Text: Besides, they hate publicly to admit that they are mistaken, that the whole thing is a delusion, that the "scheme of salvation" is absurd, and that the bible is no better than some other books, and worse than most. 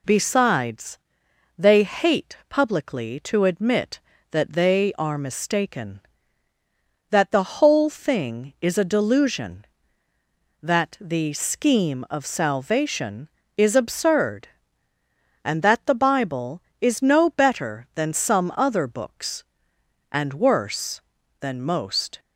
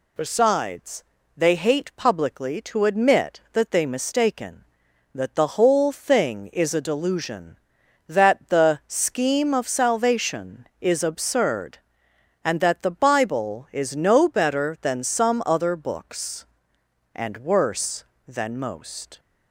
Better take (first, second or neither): first